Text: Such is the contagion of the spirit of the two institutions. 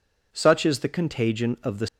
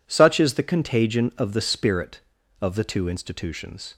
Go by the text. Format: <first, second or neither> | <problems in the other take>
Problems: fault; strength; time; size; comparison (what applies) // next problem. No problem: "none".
second | stops before "spirit of the two institutions"; at 1.8 s